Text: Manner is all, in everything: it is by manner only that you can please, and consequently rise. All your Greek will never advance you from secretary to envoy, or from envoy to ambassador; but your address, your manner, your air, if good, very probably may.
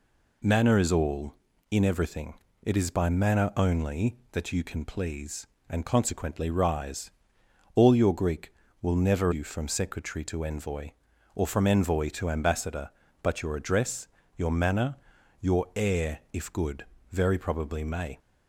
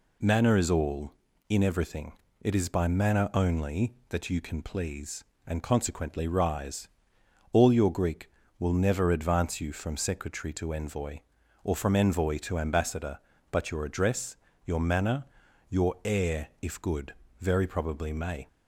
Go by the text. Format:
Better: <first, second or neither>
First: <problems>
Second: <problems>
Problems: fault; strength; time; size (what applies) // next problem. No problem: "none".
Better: second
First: skips "advance"; at 9.3 s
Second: none